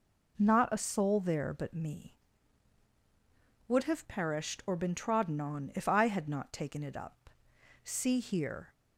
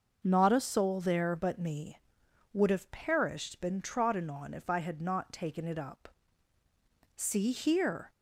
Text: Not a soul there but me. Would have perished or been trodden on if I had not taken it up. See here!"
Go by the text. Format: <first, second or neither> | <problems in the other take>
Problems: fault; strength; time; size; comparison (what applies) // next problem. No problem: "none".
first | starts louder than the rest; noticeable; until 1.2 s; 6 dB // skips "or"; at 3.5 s